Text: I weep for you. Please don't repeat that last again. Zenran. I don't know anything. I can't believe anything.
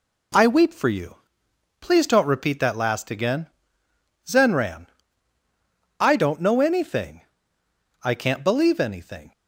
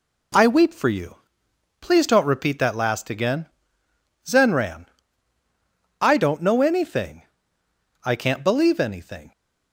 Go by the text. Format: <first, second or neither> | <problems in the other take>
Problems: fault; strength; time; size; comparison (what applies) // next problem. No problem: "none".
neither | none